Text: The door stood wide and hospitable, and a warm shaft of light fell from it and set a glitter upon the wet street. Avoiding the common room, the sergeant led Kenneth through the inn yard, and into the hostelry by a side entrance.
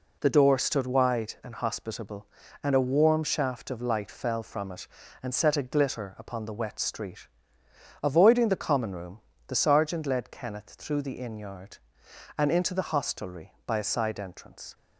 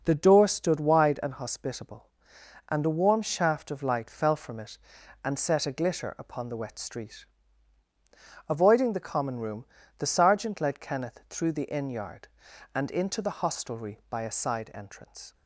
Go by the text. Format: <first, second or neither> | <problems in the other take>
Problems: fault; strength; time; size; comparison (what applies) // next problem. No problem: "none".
neither | none